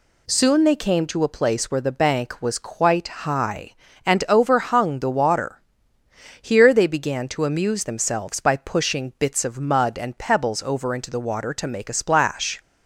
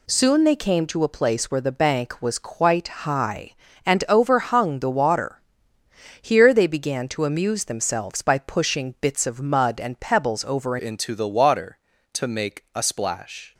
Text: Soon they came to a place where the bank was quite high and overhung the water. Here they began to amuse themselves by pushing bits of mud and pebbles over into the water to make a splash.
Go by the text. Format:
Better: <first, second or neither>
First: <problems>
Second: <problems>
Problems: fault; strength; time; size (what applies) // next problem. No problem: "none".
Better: first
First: none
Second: changes voice at "into"; from 10.7 s on; 2.8 s long